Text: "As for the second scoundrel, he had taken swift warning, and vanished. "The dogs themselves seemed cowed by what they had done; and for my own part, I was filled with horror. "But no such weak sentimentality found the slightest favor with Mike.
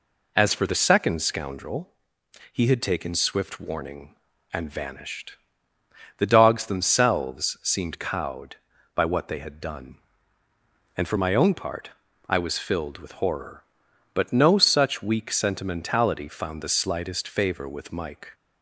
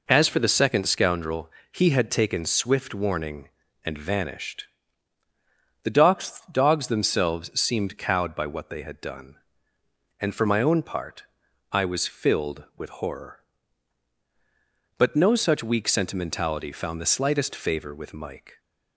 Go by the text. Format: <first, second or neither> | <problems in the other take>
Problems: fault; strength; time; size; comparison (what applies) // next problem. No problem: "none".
first | says "dogs" twice; at 6.5 s